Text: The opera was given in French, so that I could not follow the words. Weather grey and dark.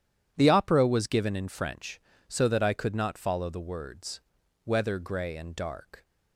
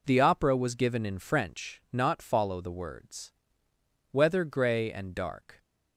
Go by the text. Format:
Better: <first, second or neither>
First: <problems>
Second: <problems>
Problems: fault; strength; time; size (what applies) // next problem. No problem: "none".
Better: first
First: none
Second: skips "so that I could"; at 1.8 s